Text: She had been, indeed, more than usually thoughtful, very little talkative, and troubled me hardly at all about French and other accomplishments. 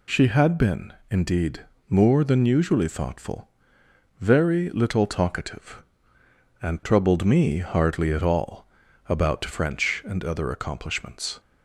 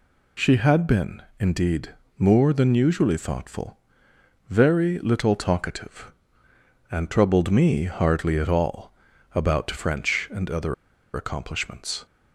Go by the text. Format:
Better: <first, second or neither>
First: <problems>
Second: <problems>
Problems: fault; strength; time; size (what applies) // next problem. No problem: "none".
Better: first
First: pauses between "all" and "about"; at 8.6 s; 0.42 s long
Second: pauses between "all" and "about"; at 8.9 s; 0.42 s long // pauses between "other" and "accomplishments"; at 10.7 s; 0.40 s long